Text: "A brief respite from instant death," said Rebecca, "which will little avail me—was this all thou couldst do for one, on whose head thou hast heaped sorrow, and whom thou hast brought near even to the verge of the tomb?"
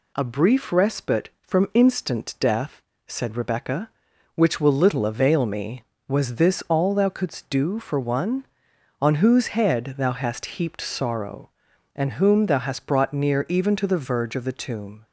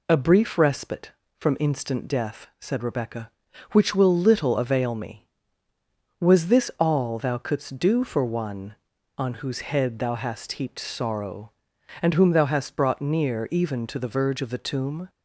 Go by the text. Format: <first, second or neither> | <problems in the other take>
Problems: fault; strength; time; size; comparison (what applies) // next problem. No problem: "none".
neither | none